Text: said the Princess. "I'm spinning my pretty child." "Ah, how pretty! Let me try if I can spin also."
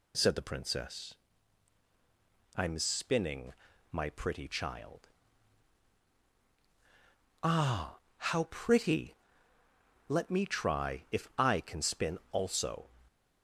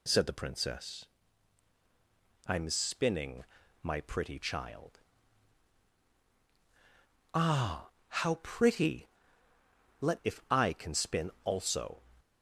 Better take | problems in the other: first | pauses between "spinning" and "my"; at 3.4 s; 0.40 s long; also in the first // skips "me try"; at 10.2 s

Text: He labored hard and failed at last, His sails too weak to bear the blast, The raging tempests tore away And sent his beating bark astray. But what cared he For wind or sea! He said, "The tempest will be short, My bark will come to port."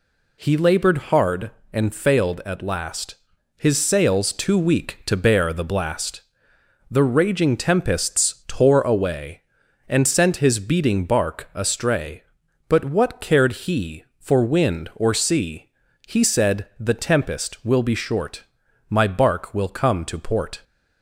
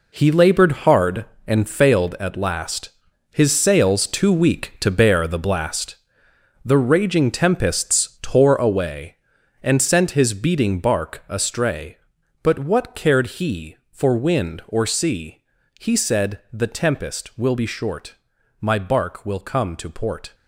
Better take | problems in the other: first | gets quieter; strong; throughout; 11 dB

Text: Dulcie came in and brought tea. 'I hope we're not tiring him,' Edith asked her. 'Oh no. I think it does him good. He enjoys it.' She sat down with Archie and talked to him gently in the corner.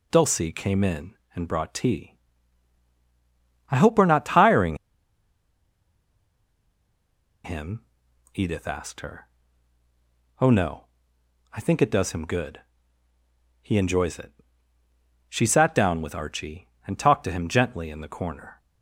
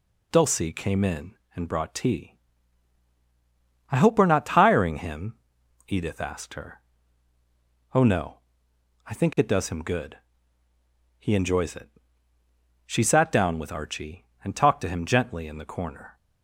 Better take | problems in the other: second | pauses between "tiring" and "him"; strong; at 4.7 s; 2.6 s long

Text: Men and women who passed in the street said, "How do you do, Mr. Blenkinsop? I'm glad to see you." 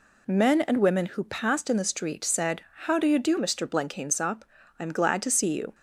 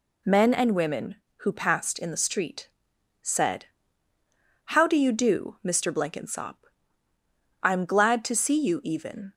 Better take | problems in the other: first | pauses between "street" and "said"; noticeable; at 2.6 s; 0.52 s long // goes on to say "Even"; slight; from 8.8 s on; 0.48 s long

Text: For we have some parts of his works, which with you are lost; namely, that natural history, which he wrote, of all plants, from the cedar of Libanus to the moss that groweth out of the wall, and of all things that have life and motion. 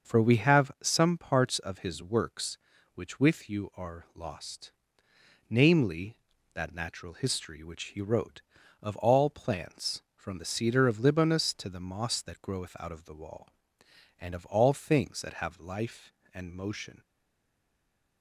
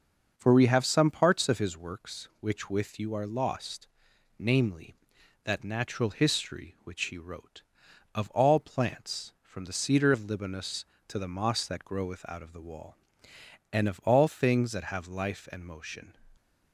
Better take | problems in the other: second | starts louder than the rest; until 1.2 s; 6.5 dB; also in the second // stays silent after the last word; noticeable; from 17.0 s on; 1.2 s long

